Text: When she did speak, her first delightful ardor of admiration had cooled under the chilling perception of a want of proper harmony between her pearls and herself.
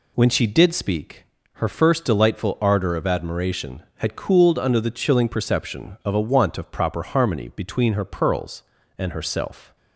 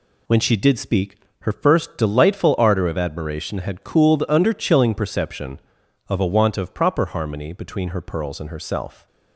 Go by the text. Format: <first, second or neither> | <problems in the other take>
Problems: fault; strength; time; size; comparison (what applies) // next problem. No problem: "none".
first | skips "the"; at 4.5 s